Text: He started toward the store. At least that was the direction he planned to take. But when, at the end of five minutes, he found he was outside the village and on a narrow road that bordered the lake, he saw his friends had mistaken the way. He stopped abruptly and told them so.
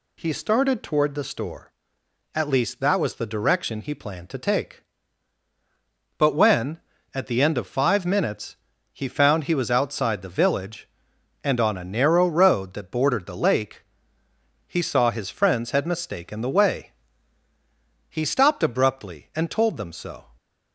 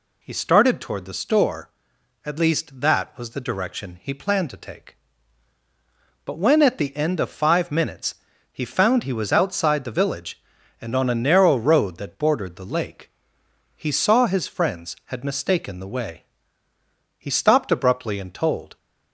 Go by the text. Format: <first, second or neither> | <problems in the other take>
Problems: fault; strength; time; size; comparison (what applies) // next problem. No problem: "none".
first | stops before "them so"; at 18.7 s